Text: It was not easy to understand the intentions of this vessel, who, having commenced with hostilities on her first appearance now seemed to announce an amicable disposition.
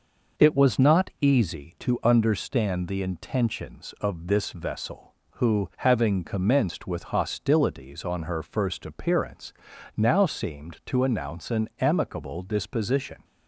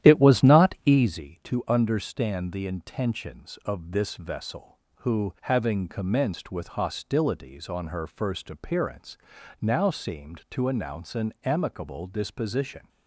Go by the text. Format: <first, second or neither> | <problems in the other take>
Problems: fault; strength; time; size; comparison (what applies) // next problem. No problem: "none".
first | starts louder than the rest; strong; until 1.1 s; 11.5 dB // pauses between "appearance" and "now"; at 9.1 s; 0.42 s long; also in the first